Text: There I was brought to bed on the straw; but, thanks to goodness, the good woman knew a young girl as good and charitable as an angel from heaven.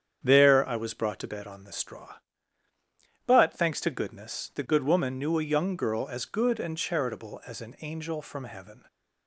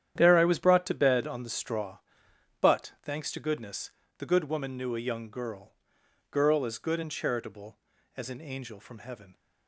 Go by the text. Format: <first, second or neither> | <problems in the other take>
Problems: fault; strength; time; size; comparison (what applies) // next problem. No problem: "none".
first | starts louder than the rest; strong; until 1.1 s; 10 dB; strong in the first // says "girl" twice; at 6.3 s